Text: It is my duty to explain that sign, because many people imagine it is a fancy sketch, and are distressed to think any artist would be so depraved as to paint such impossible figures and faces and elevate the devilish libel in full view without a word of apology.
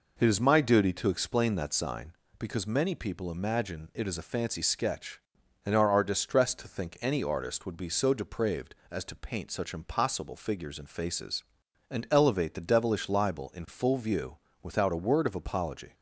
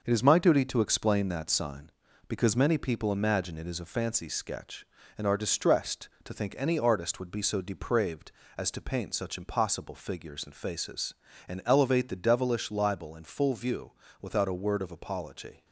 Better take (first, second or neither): second